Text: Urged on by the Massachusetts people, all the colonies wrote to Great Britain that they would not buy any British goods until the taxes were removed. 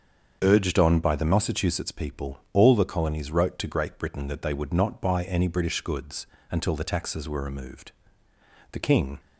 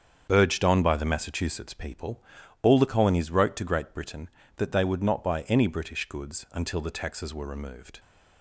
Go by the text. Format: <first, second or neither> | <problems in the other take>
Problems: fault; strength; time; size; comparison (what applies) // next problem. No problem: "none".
second | starts louder than the rest; until 1.4 s; 7 dB; strong in the second // pauses between "goods" and "until"; slight; at 6.2 s; 0.24 s long // goes on to say "The king"; slight; from 8.7 s on; 0.48 s long